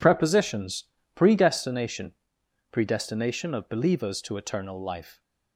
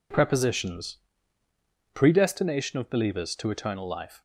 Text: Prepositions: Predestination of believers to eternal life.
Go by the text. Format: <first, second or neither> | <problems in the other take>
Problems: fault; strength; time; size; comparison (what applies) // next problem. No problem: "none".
second | says "Predestination" twice; at 2.7 s